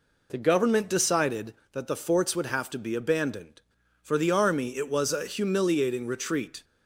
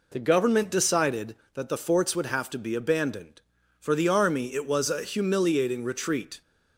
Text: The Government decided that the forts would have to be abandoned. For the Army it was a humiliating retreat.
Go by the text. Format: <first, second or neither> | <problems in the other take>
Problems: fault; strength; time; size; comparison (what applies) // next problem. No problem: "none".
neither | none